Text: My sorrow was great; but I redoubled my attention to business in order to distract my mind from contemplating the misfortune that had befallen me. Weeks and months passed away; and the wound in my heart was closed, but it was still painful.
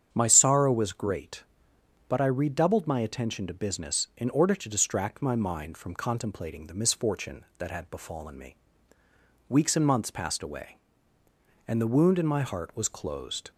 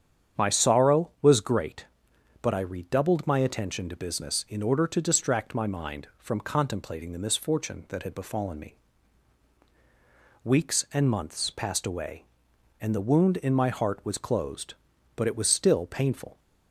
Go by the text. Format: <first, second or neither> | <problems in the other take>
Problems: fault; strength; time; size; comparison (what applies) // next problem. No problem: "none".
second | starts louder than the rest; strong; until 1.1 s; 8 dB; strong in the second // stops before "but it was still painful"; at 13.5 s